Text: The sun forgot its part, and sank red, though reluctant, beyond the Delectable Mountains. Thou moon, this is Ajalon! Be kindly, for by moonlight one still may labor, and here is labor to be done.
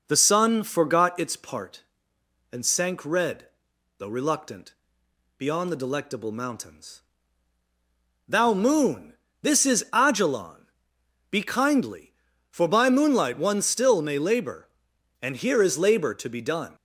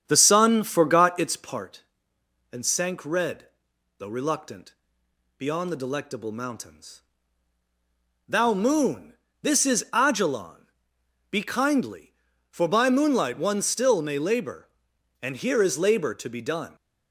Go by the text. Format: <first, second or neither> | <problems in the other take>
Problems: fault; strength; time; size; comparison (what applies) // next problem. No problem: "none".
first | starts louder than the rest; strong; until 1.7 s; 8.5 dB